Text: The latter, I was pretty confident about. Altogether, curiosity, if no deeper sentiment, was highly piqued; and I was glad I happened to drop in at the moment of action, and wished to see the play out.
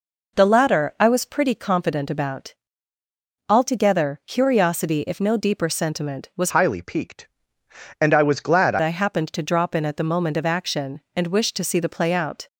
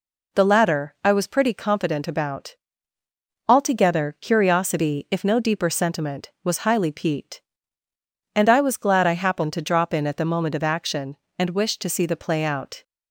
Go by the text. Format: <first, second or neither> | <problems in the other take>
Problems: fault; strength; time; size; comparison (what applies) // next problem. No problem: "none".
second | changes voice from "highly" to "glad"; from 6.5 to 8.7 s; 2.2 s long